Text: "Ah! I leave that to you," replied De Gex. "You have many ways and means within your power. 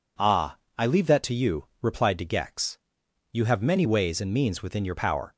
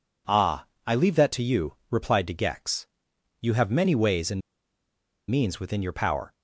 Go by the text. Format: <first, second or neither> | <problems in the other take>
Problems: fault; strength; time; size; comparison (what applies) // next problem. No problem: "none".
first | pauses between "and" and "means"; noticeable; at 4.4 s; 0.89 s long